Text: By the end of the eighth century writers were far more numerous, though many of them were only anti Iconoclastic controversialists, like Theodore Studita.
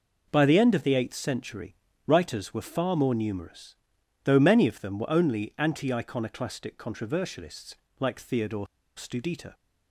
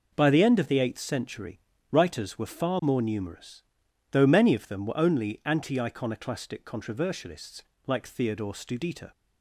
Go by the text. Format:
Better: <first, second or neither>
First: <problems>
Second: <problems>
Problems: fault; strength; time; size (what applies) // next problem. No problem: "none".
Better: second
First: pauses between "century" and "writers"; slight; at 1.7 s; 0.32 s long // pauses between "Theodore" and "Studita"; slight; at 8.6 s; 0.30 s long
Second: pauses between "century" and "writers"; slight; at 1.5 s; 0.32 s long